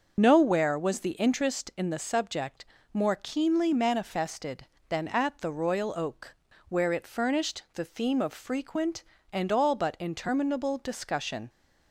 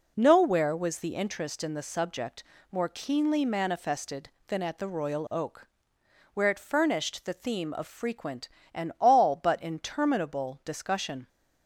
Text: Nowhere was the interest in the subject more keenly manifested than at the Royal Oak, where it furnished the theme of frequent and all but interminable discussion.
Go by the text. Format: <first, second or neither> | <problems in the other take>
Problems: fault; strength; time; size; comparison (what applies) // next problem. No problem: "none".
second | loses the start of "Nowhere"; at 0.1 s; 45 ms // starts louder than the rest; until 1.1 s; 6.5 dB // pauses between "subject" and "more"; slight; at 2.6 s; 0.30 s long; slight in the second